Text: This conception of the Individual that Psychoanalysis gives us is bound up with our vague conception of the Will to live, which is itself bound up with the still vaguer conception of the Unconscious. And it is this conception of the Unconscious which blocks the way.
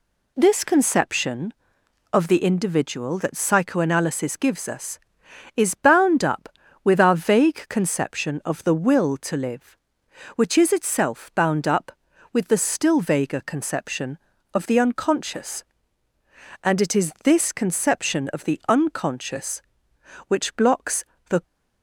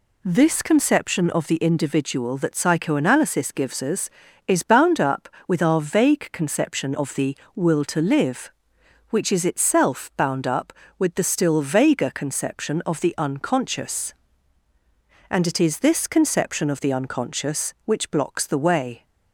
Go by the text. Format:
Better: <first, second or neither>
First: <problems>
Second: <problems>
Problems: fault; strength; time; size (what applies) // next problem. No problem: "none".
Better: second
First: pauses between "blocks" and "the"; slight; at 21.0 s; 0.26 s long // stops before "way"; at 21.4 s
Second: none